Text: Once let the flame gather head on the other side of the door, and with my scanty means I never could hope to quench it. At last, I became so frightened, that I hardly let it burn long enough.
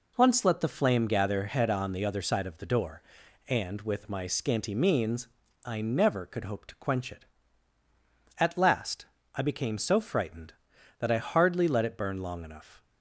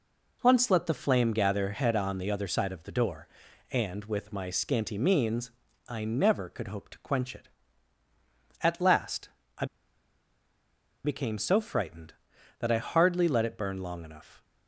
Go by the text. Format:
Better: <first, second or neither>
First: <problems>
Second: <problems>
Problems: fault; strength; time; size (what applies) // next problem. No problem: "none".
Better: first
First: pauses between "means" and "I"; at 5.2 s; 0.38 s long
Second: pauses between "means" and "I"; at 5.5 s; 0.38 s long // pauses between "I" and "became"; strong; at 9.6 s; 1.3 s long